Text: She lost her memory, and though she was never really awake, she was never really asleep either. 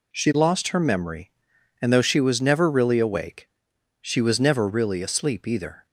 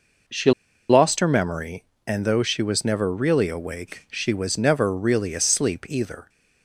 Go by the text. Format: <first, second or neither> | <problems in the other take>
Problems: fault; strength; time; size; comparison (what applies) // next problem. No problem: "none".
first | pauses between "She" and "lost"; at 0.5 s; 0.39 s long